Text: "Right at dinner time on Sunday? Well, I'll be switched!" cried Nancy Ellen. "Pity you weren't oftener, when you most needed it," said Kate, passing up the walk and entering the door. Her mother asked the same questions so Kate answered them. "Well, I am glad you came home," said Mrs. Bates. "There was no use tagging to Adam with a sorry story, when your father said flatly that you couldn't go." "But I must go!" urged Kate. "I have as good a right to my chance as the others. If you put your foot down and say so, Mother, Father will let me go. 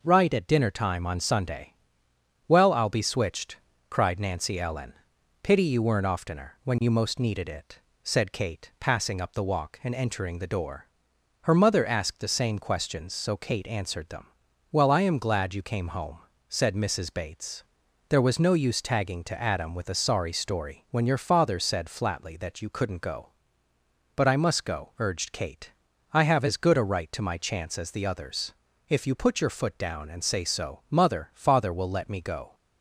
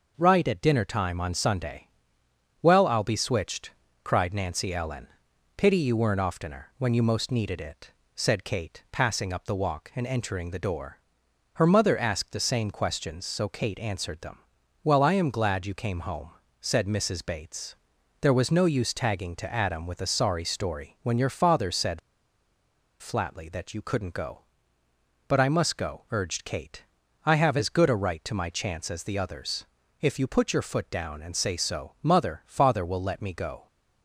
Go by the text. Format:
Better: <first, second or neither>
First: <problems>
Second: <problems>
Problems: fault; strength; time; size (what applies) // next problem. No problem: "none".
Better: first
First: none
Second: pauses between "said" and "flatly"; at 21.9 s; 1.0 s long